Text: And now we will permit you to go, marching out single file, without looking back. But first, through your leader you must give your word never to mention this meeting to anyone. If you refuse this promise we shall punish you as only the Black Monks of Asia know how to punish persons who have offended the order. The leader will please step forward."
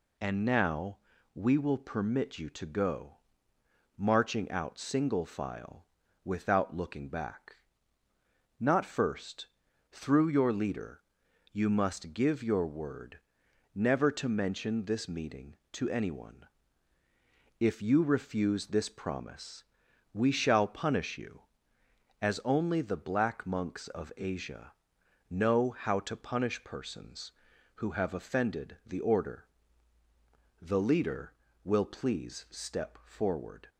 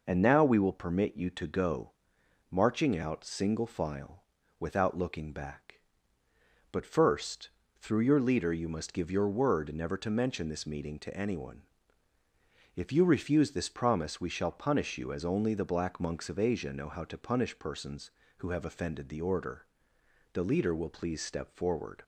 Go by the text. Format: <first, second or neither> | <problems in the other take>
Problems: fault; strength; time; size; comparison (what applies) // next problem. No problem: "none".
second | pauses between "now" and "we"; slight; at 0.9 s; 0.36 s long // says "Not" for "But"; at 8.5 s // pauses between "leader" and "you"; noticeable; at 11.0 s; 0.50 s long // pauses between "word" and "never"; noticeable; at 13.1 s; 0.56 s long // pauses between "promise" and "we"; noticeable; at 19.6 s; 0.48 s long // pauses between "Asia" and "know"; noticeable; at 24.7 s; 0.58 s long